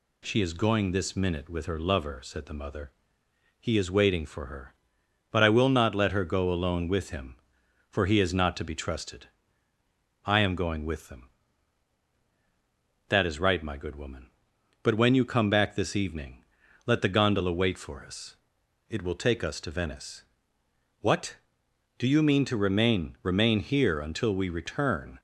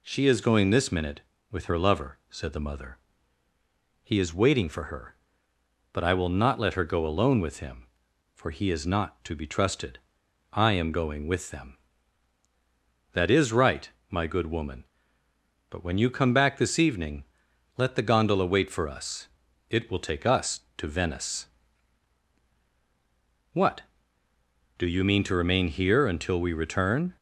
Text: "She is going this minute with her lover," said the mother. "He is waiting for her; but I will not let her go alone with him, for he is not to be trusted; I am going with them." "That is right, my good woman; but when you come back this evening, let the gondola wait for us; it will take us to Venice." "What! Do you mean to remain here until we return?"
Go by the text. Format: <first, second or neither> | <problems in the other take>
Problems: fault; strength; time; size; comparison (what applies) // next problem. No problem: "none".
second | says "remain" twice; at 23.2 s